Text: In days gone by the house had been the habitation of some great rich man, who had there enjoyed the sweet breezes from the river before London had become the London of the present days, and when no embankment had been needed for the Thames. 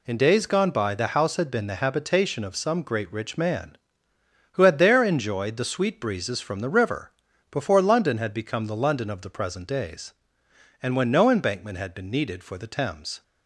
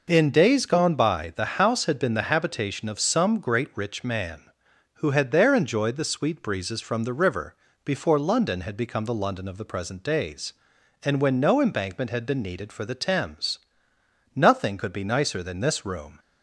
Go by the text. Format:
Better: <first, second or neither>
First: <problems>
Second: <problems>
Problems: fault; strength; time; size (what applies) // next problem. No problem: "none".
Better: first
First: pauses between "river" and "before"; at 7.1 s; 0.40 s long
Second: pauses between "river" and "before"; slight; at 7.5 s; 0.30 s long // goes on to say "Nothing could be nicer than this room"; strong; from 14.3 s on; 1.8 s long